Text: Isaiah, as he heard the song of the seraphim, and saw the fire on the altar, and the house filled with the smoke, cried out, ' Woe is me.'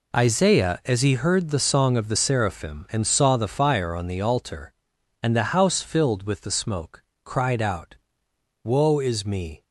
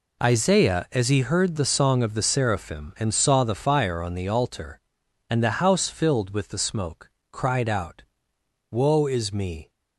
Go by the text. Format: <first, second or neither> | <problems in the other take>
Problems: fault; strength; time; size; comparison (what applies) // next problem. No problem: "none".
neither | none